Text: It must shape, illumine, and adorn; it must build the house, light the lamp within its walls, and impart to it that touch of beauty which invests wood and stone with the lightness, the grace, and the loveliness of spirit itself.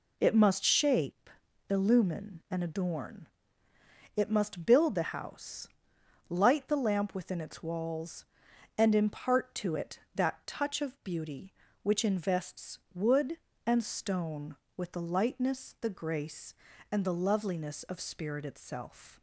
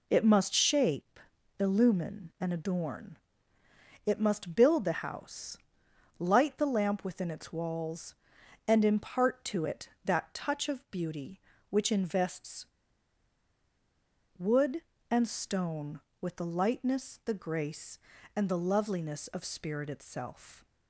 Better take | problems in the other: first | pauses between "invests" and "wood"; strong; at 12.6 s; 1.7 s long

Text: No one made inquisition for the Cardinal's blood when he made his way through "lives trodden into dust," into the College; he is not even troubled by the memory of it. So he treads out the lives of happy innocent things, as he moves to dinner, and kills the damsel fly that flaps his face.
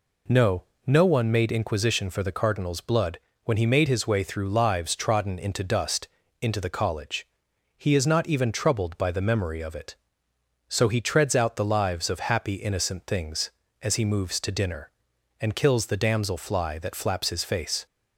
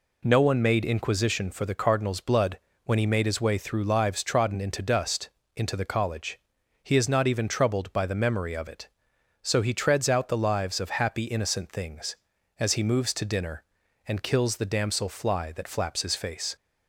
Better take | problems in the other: second | says "No" twice; at 0.8 s // pauses between "blood" and "when"; slight; at 3.1 s; 0.24 s long; slight in the second

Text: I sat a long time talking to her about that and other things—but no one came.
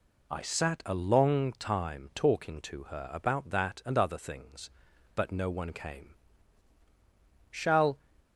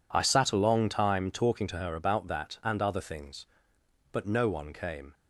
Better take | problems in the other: second | goes on to say "Shall"; slight; from 7.5 s on; 0.48 s long

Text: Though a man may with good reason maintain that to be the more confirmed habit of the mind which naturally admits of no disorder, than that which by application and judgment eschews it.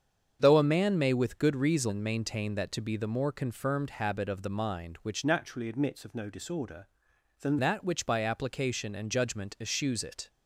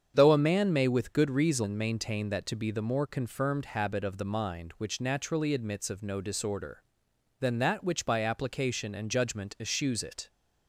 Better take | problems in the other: second | starts louder than the rest; strong; until 1.4 s; 7.5 dB; strong in the second // changes voice from "naturally" to "than"; from 5.2 to 7.5 s; 2.3 s long

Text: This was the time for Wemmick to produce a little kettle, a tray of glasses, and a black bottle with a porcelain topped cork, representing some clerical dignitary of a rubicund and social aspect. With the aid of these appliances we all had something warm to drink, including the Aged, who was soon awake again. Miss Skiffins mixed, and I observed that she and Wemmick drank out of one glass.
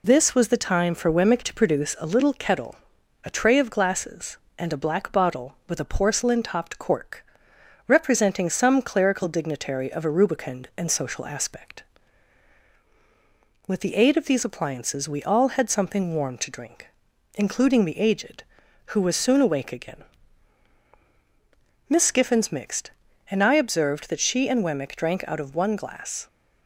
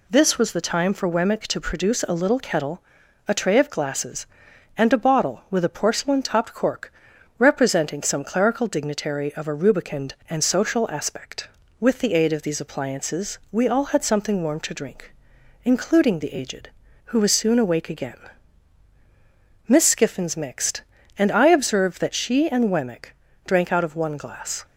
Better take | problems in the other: first | skips "black"; at 4.9 s // pauses between "Wemmick" and "drank"; slight; at 23.1 s; 0.32 s long

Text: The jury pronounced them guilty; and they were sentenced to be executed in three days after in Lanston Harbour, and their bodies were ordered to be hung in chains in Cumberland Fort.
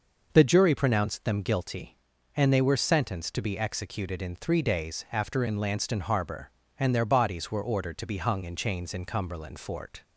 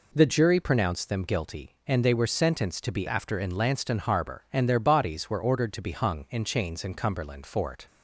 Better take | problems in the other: first | skips "executed in three days"; at 3.0 s

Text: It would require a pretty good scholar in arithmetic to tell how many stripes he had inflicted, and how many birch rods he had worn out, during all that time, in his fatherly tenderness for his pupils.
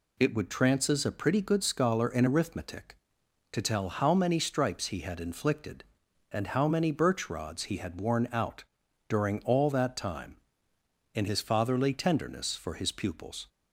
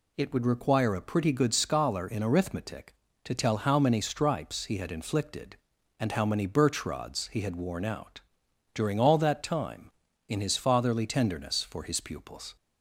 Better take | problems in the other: second | says "trances" for "require"; at 0.4 s

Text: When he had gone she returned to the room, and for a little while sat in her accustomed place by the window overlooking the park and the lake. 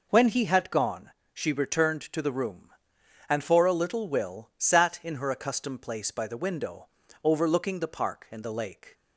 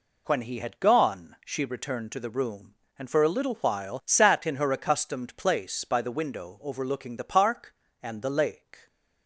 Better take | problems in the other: second | pauses between "gone" and "she"; slight; at 1.1 s; 0.22 s long // says "will" for "while"; at 4.0 s // pauses between "window" and "overlooking"; slight; at 6.8 s; 0.36 s long

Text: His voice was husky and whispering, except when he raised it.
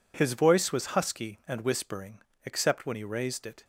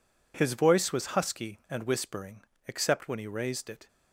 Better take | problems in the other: neither | none

